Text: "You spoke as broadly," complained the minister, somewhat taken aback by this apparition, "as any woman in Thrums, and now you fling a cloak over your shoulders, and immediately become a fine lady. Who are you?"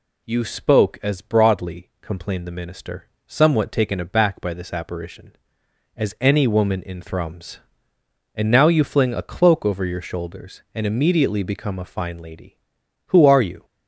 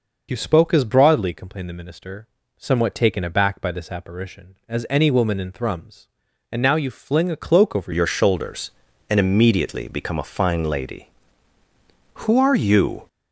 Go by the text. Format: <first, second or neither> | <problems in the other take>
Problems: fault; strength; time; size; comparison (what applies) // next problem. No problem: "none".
first | changes voice at "your"; from 7.9 s on; 5.1 s long